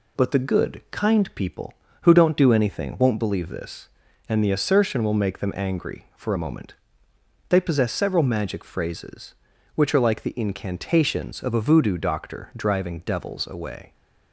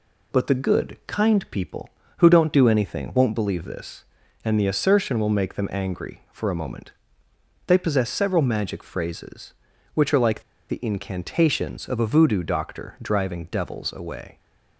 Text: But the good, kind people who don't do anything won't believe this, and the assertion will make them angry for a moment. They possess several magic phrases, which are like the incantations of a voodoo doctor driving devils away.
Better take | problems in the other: first | pauses between "like" and "the"; slight; at 10.4 s; 0.27 s long

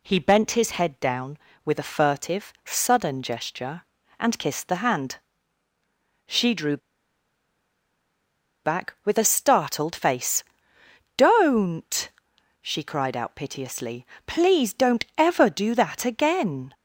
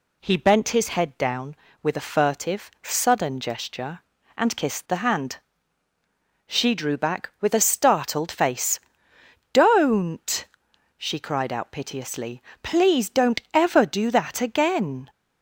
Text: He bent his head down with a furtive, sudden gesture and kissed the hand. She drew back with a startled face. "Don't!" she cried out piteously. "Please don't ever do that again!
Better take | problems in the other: second | pauses between "drew" and "back"; strong; at 6.7 s; 1.8 s long

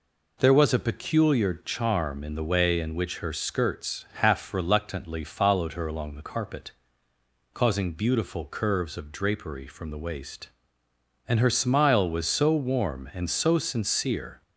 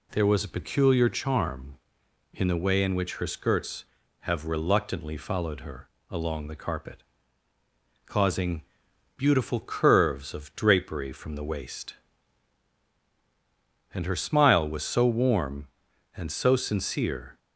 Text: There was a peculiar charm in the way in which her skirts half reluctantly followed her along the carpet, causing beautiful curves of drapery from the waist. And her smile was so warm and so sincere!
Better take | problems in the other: first | says "have" for "half"; at 4.2 s // pauses between "her" and "along"; slight; at 5.8 s; 0.22 s long // pauses between "causing" and "beautiful"; noticeable; at 8.6 s; 0.56 s long

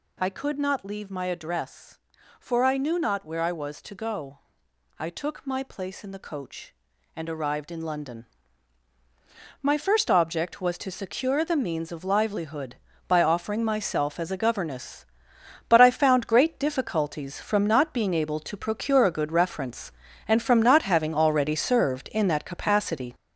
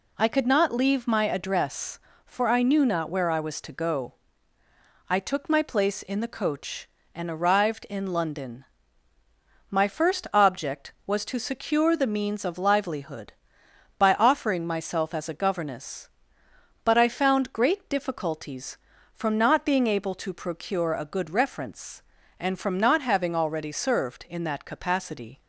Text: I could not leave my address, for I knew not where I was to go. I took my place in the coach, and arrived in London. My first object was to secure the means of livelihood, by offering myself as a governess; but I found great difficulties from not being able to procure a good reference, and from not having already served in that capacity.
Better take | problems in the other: second | gets louder; throughout; 6.5 dB

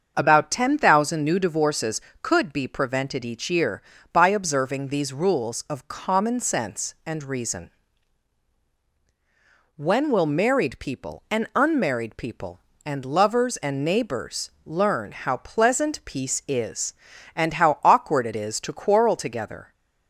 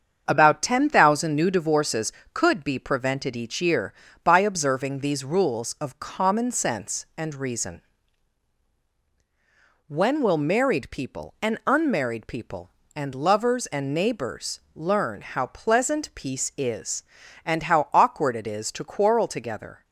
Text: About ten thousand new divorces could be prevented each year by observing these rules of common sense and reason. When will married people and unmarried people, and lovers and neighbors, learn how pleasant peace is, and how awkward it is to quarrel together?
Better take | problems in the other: first | gets quieter; noticeable; throughout; 5.5 dB // starts louder than the rest; strong; until 1.2 s; 7 dB; also in the first

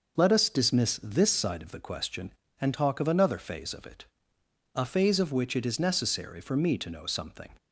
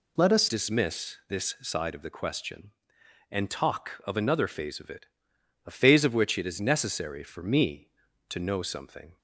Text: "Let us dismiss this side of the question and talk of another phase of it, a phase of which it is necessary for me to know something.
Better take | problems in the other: first | changes voice at "dismiss"; from 0.4 s on; 8.7 s long

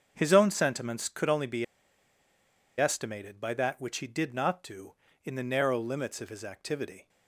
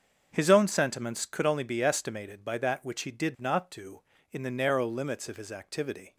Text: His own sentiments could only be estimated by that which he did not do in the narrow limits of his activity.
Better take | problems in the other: second | starts louder than the rest; until 1.1 s; 7 dB; also in the second // pauses between "be" and "estimated"; at 1.6 s; 1.1 s long

